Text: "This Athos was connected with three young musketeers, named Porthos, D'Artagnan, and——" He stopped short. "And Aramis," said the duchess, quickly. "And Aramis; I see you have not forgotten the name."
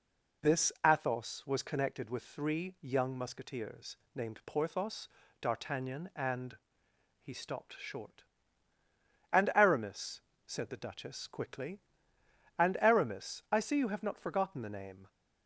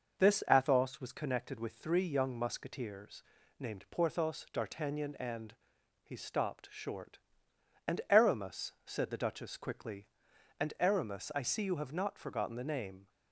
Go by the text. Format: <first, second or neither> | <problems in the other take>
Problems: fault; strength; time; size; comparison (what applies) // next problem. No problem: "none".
neither | none